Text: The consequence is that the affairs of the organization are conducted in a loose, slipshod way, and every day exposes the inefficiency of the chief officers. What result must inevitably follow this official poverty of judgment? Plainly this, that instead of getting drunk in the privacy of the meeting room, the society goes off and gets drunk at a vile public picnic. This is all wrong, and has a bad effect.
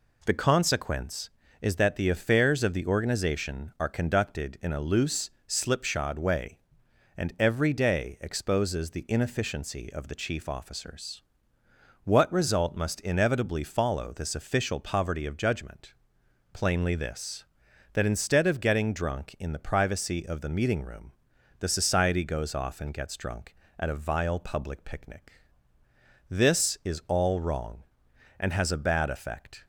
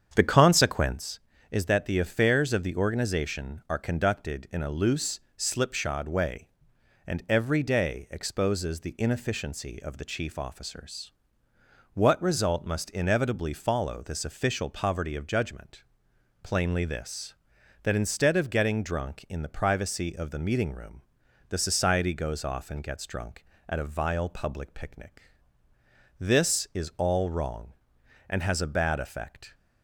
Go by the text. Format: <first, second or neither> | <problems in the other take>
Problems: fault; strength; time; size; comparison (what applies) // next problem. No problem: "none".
first | starts louder than the rest; strong; until 1.0 s; 8 dB